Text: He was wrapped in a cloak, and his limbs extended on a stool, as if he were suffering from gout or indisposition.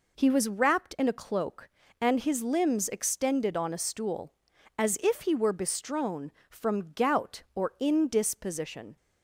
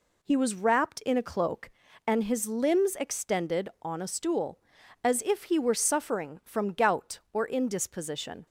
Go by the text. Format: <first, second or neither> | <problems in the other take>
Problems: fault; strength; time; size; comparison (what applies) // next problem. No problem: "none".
second | says "bestrown" for "suffering"; at 5.5 s